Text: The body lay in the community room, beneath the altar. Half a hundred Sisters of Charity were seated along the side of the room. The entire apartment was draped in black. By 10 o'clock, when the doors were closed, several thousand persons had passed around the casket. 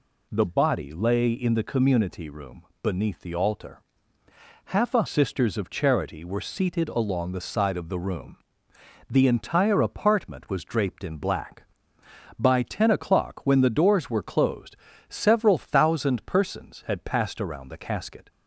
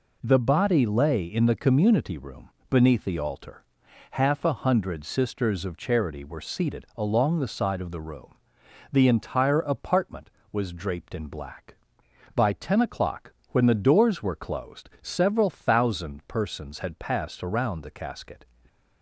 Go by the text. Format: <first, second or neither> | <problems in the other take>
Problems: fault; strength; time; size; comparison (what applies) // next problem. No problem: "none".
second | skips "hundred"; at 5.0 s